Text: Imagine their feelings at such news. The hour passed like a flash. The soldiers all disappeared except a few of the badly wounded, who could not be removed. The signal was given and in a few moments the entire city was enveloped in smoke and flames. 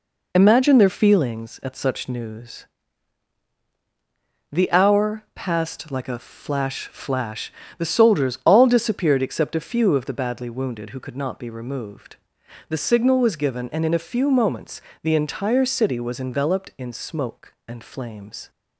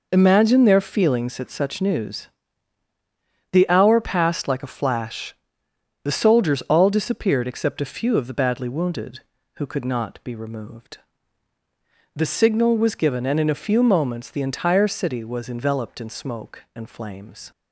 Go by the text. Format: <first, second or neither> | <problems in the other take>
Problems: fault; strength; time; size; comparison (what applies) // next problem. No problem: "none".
second | says "flash" twice; at 6.8 s // pauses between "moments" and "the"; slight; at 14.7 s; 0.22 s long